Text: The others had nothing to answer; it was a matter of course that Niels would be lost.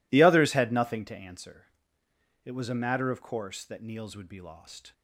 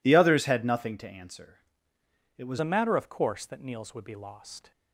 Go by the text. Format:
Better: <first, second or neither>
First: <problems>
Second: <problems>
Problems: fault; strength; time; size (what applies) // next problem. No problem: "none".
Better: first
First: none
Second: changes voice at "a"; from 2.5 s on; 2.2 s long